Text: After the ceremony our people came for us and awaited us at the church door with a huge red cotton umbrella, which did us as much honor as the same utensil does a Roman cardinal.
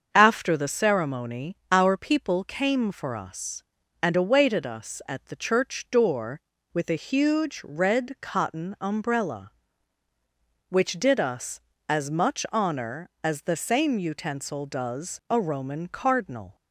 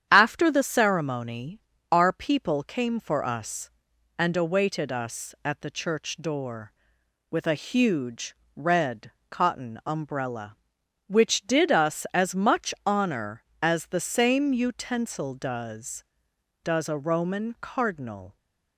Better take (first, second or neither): first